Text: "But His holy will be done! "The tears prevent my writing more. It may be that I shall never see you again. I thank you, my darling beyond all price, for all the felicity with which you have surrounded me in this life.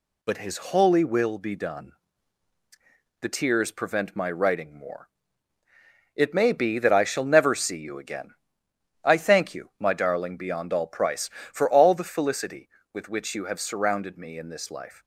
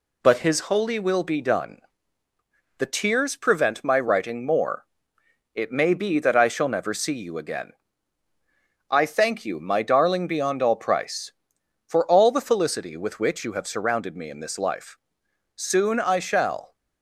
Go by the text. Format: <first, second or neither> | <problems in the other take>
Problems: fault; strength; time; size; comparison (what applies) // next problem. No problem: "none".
first | goes on to say "Soon I shall"; noticeable; from 15.5 s on; 1.2 s long